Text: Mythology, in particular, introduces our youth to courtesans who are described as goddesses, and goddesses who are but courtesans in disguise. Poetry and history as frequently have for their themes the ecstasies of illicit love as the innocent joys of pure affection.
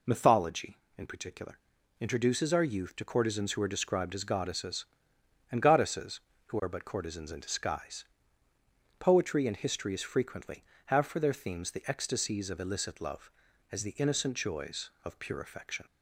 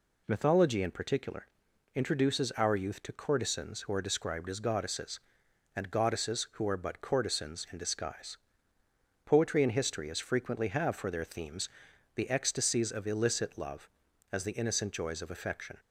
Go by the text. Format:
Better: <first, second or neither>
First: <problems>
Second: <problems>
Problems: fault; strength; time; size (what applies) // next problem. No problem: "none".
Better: first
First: none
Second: pauses between "themes" and "the"; noticeable; at 11.6 s; 0.48 s long // skips "pure"; at 15.3 s